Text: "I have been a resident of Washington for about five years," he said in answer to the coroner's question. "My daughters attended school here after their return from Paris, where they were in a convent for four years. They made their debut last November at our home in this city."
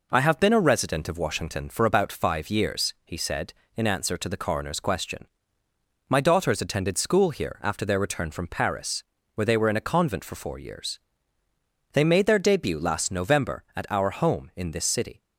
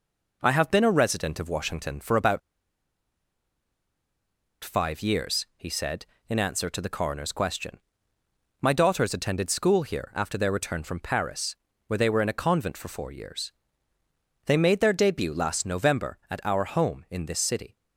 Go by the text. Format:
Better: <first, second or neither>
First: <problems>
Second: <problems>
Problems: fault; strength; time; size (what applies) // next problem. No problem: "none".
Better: first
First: none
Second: pauses between "about" and "five"; strong; at 2.4 s; 2.2 s long